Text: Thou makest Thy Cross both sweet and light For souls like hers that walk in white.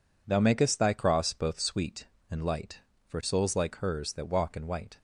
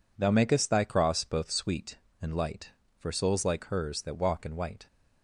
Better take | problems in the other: neither | none

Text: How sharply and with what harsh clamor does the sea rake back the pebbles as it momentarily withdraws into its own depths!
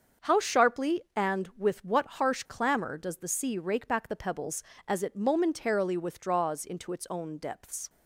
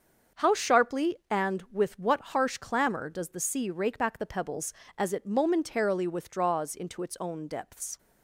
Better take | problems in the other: neither | starts louder than the rest; the same in both

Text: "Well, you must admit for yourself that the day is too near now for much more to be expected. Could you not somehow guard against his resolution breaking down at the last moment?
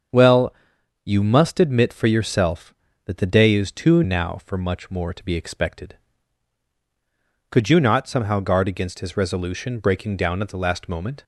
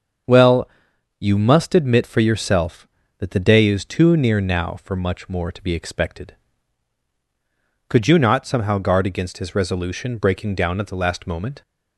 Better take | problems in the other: second | starts louder than the rest; strong; until 1.6 s; 7.5 dB; strong in the second // skips "near"; at 4.0 s

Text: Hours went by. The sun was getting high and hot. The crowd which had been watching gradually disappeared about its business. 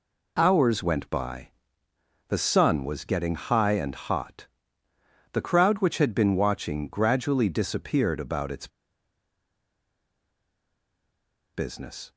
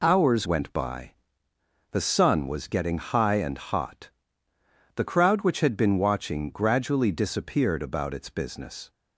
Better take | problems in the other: second | pauses between "its" and "business"; strong; at 8.6 s; 2.8 s long

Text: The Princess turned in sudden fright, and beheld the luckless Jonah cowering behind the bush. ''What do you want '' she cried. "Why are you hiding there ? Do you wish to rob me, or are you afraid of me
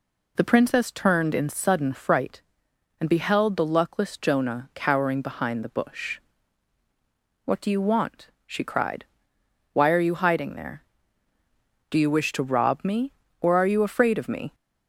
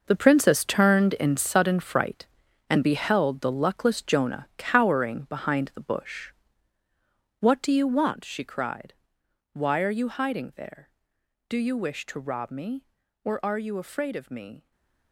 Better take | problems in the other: first | gets quieter; strong; throughout; 13 dB // stays silent after the last word; slight; from 14.5 s on; 0.6 s long

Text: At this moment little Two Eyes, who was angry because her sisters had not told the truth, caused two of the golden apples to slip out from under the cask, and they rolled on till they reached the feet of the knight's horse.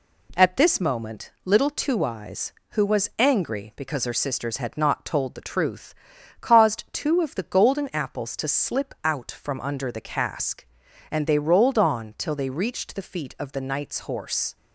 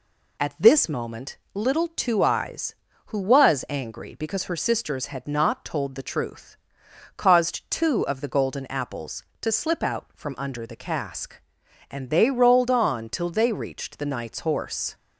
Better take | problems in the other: first | pauses between "moment" and "little"; slight; at 1.3 s; 0.16 s long // skips "feet of the"; at 14.0 s

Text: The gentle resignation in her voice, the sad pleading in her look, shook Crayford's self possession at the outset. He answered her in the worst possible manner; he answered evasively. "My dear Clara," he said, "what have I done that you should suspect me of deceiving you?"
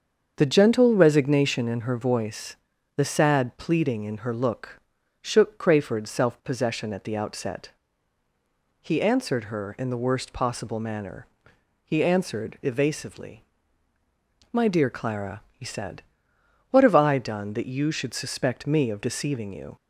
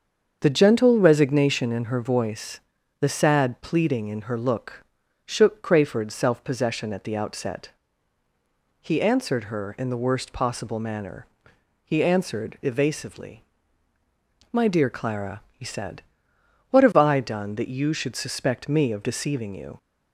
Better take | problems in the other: neither | starts louder than the rest; strong; the same in both

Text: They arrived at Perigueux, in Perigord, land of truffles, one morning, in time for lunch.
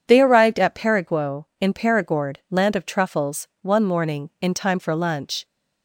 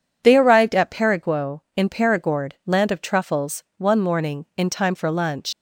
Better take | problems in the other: first | leaves "lunch" unfinished; at 5.5 s; 85 ms

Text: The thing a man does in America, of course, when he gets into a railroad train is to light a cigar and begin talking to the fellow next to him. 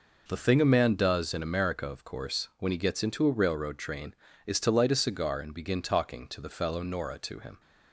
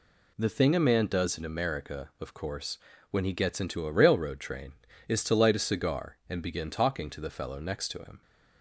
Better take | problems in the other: second | says "nora" for "next"; at 6.8 s

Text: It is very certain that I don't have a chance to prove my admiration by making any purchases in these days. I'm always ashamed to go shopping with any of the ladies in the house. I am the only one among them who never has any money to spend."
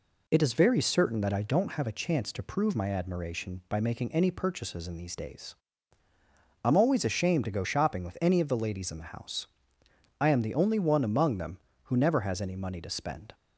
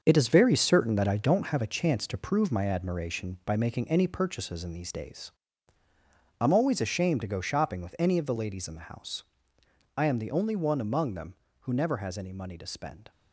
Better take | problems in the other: first | gets quieter; strong; throughout; 8.5 dB

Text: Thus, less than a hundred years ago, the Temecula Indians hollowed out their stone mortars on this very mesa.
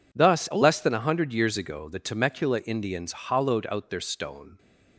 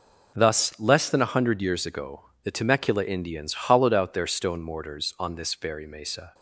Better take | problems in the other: second | stops before "mortars on this very mesa"; at 4.5 s

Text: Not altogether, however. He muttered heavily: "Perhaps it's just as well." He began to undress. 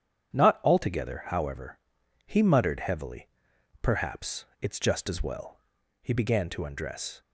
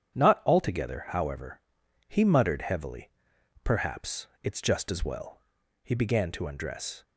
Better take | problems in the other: neither | starts louder than the rest; strong; the same in both // pauses between "Perhaps" and "it's"; slight; the same in both

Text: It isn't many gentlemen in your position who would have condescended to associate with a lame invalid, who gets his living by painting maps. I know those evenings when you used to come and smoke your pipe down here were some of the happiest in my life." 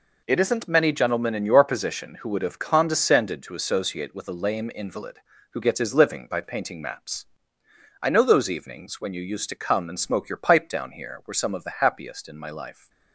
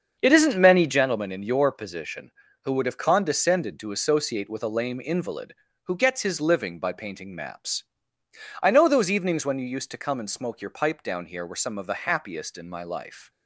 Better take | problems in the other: first | starts louder than the rest; until 1.1 s; 7 dB

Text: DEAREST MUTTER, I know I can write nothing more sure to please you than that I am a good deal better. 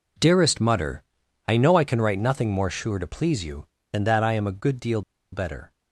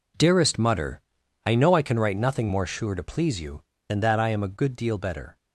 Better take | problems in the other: second | pauses between "deal" and "better"; slight; at 5.0 s; 0.30 s long

